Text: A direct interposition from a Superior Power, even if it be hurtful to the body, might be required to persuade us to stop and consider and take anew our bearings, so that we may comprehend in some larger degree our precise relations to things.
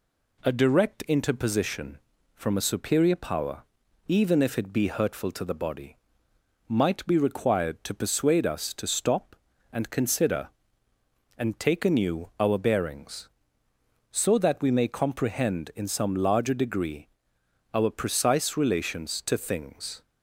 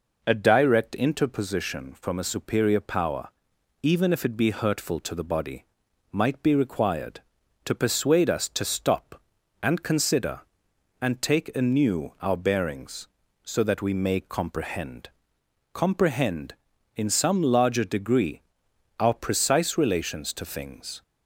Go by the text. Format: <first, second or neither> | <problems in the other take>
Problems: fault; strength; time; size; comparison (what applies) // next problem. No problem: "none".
first | says "comprehend" twice; at 15.7 s // pauses between "degree" and "our"; noticeable; at 18.4 s; 0.58 s long; noticeable in the first